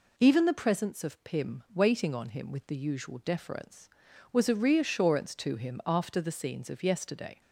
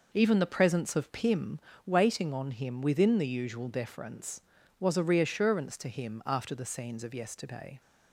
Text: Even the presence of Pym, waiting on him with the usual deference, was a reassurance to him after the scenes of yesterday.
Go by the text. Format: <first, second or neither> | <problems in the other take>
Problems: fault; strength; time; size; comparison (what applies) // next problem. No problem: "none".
first | says "within" for "with"; at 2.8 s